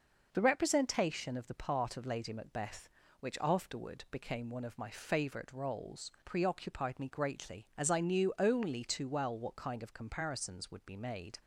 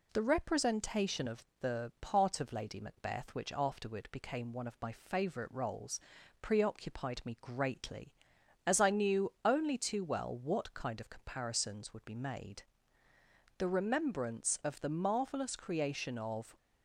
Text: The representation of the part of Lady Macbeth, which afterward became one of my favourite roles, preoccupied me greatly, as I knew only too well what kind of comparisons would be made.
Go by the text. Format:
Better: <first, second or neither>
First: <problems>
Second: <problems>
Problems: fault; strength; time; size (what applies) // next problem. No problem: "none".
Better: first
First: none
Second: pauses between "of" and "the"; slight; at 1.4 s; 0.16 s long // goes on to say "The remembrance of the marvellous creation of"; strong; from 13.5 s on; 3.0 s long